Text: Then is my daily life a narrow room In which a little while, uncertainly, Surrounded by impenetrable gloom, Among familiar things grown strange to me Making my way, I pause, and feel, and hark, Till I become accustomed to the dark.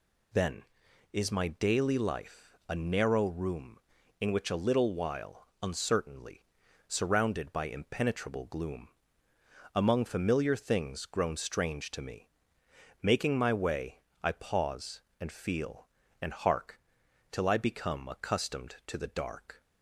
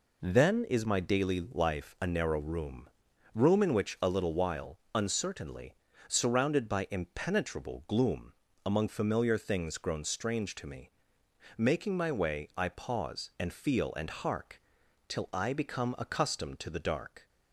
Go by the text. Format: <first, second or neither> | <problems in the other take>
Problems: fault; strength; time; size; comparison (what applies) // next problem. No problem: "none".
first | says "room" twice; at 3.3 s // pauses between "me" and "Making"; noticeable; at 10.8 s; 0.66 s long; noticeable in the first